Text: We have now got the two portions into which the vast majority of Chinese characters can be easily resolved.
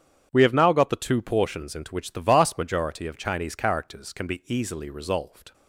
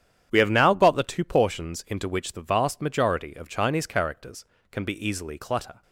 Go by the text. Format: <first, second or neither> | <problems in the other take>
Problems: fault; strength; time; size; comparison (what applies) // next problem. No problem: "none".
first | starts louder than the rest; strong; until 1.3 s; 9.5 dB; strong in the first // says "clutter" for "resolved"; at 5.3 s